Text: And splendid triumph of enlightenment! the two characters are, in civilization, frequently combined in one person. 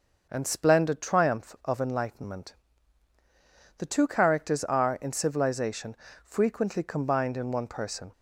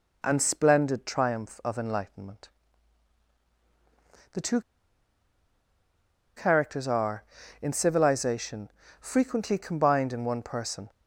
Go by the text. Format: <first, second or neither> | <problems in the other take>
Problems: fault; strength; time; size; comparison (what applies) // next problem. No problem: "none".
first | pauses between "two" and "characters"; strong; at 4.5 s; 1.7 s long